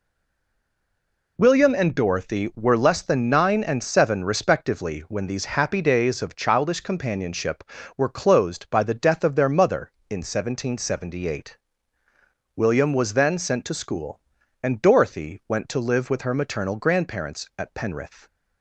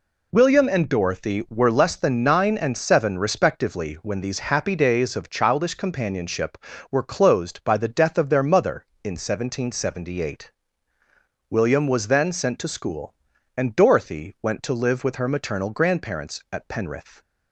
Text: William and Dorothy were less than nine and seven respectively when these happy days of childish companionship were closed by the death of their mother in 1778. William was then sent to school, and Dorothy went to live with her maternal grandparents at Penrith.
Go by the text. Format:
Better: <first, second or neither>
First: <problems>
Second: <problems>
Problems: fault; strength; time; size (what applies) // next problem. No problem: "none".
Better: second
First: stays silent before the first word; noticeable; until 1.3 s; 1.3 s long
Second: none